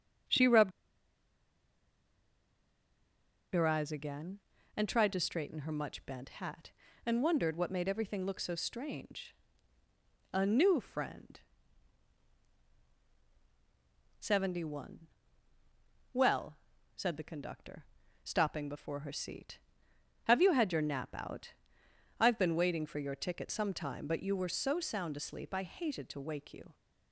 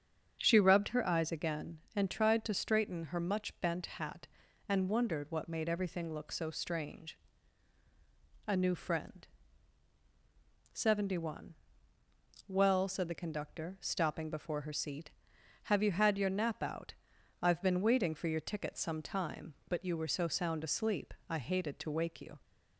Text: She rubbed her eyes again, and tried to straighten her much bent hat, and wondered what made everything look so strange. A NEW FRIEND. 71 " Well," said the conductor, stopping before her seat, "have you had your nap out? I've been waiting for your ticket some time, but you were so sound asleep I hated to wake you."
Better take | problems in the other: second | starts louder than the rest; strong; until 4.1 s; 7.5 dB; strong in the second // pauses between "rubbed" and "her"; strong; at 0.7 s; 2.8 s long

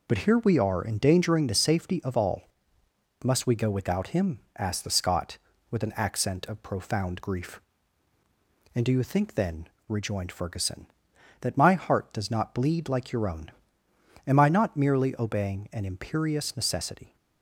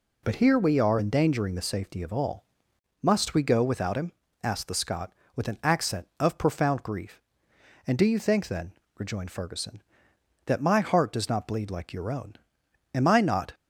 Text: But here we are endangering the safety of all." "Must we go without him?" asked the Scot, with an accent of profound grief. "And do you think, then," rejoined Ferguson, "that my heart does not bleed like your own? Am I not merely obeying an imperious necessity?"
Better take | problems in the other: first | stops before "merely obeying an imperious necessity"; at 13.5 s

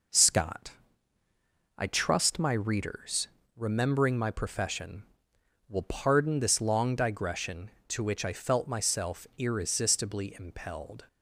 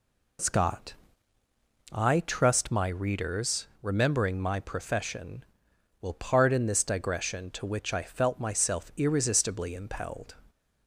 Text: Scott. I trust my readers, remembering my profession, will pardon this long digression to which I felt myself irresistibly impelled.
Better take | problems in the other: first | skips "long"; at 6.8 s

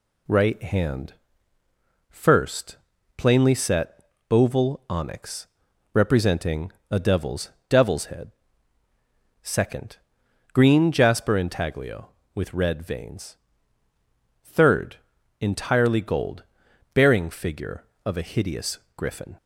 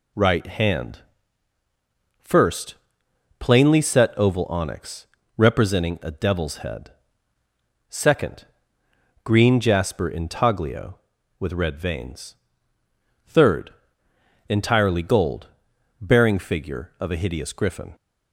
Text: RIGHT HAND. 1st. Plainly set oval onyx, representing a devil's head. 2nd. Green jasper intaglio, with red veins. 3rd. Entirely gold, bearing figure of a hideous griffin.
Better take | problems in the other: second | pauses between "set" and "oval"; slight; at 4.0 s; 0.28 s long // pauses between "representing" and "a"; slight; at 6.7 s; 0.18 s long // says "devil's" twice; at 7.6 s // pauses between "hideous" and "griffin"; slight; at 18.7 s; 0.16 s long

